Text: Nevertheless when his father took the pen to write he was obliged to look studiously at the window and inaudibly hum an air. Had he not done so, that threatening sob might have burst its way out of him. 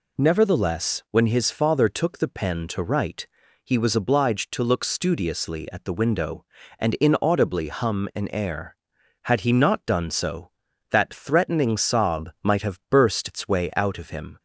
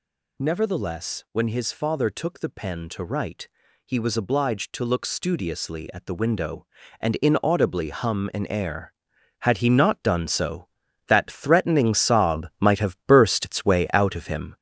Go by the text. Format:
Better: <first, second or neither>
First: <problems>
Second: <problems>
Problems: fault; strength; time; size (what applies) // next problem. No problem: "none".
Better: first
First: pauses between "write" and "he"; at 3.2 s; 0.38 s long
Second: gets louder; strong; throughout; 7.5 dB // pauses between "write" and "he"; at 3.4 s; 0.38 s long